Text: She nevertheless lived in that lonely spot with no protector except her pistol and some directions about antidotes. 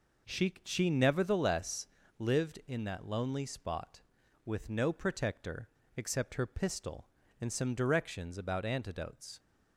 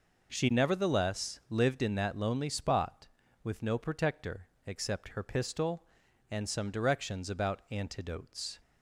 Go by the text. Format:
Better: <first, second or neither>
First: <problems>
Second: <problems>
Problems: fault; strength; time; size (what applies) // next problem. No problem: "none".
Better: second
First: says "She" twice; at 0.6 s // pauses between "nevertheless" and "lived"; slight; at 1.8 s; 0.30 s long // pauses between "protector" and "except"; slight; at 5.6 s; 0.26 s long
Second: pauses between "protector" and "except"; slight; at 4.4 s; 0.18 s long